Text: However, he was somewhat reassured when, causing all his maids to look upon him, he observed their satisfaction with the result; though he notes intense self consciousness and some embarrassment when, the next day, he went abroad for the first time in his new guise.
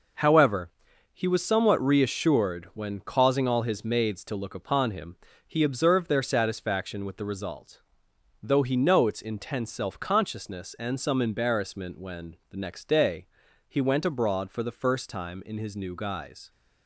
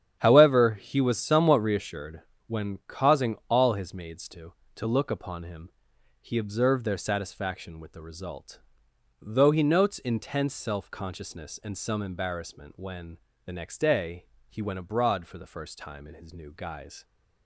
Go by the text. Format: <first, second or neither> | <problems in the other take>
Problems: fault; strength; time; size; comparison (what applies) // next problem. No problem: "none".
first | starts louder than the rest; strong; until 1.2 s; 9.5 dB // pauses between "reassured" and "when"; slight; at 2.2 s; 0.26 s long // says "to" twice; at 4.7 s